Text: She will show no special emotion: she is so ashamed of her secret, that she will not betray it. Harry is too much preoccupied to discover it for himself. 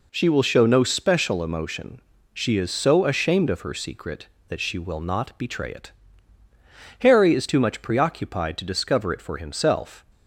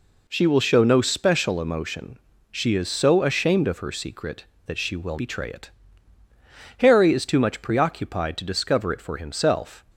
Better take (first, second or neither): first